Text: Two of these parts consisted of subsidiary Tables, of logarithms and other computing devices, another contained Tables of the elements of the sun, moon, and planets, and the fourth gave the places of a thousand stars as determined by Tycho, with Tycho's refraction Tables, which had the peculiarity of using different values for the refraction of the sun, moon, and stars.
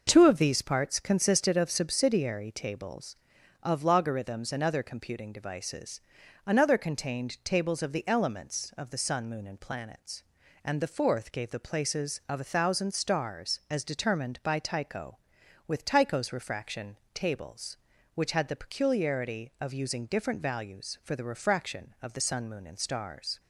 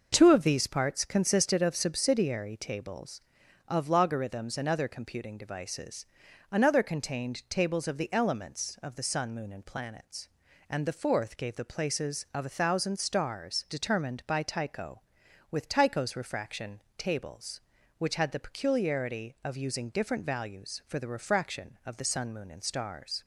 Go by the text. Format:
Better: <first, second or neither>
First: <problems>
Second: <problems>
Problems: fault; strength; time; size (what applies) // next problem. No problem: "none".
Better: first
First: pauses between "refraction" and "Tables"; slight; at 16.9 s; 0.16 s long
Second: skips "as"; at 13.6 s // pauses between "refraction" and "Tables"; slight; at 16.7 s; 0.16 s long